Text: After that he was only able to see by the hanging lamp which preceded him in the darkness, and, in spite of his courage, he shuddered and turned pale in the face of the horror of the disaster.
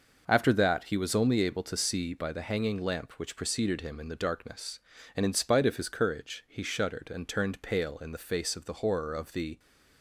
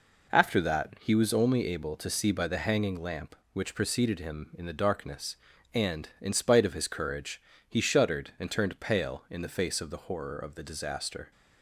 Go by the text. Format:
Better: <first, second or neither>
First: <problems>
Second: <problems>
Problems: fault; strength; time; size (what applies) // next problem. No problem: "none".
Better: second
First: stops before "disaster"; at 9.5 s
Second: none